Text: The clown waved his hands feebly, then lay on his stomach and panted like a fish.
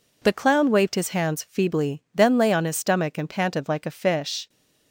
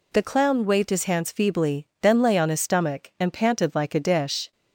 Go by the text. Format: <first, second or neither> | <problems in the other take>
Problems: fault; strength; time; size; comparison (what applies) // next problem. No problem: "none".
first | says "dish" for "fish"; at 3.9 s